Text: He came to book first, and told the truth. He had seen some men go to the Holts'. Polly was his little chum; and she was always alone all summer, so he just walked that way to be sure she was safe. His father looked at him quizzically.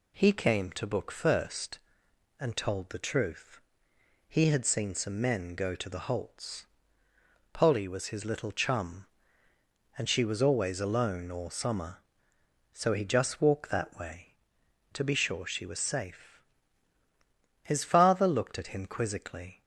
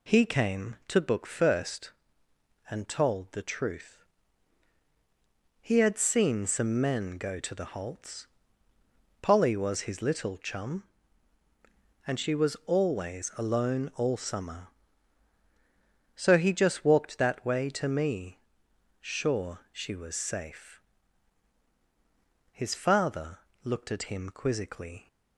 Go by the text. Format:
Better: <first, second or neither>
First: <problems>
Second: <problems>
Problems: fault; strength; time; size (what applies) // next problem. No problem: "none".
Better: first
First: none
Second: says "me" for "be"; at 17.8 s // pauses between "father" and "looked"; slight; at 23.3 s; 0.26 s long